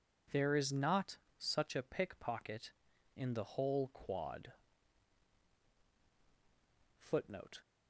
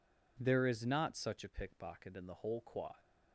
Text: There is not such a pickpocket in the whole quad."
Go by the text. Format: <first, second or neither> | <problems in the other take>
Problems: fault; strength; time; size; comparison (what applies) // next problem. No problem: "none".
second | pauses between "not" and "such"; slight; at 1.1 s; 0.22 s long // goes on to say "Footnote"; noticeable; from 6.9 s on; 0.62 s long